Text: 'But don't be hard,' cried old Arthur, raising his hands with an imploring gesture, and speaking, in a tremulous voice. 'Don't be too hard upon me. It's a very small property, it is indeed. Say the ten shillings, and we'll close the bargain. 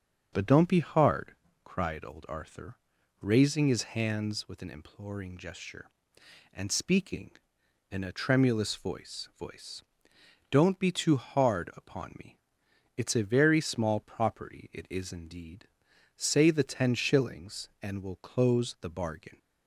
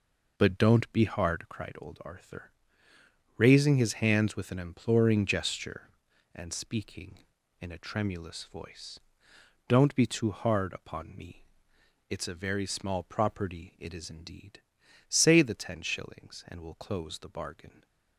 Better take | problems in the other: second | starts louder than the rest; until 1.3 s; 6.5 dB // says "voice" twice; at 9.3 s

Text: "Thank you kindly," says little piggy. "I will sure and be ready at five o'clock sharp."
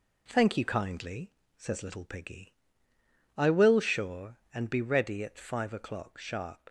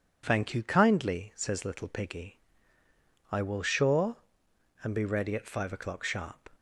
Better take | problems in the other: neither | none

